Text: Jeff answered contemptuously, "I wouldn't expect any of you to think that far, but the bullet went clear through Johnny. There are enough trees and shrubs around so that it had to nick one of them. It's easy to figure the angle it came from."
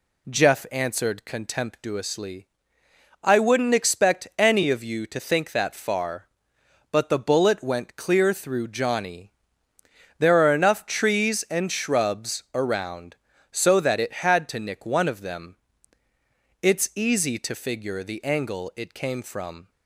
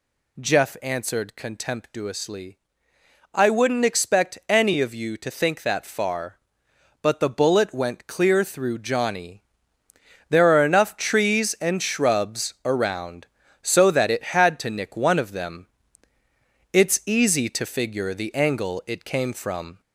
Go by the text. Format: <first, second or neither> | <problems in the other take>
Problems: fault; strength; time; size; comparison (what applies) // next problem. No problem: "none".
first | gets louder; slight; throughout; 2.5 dB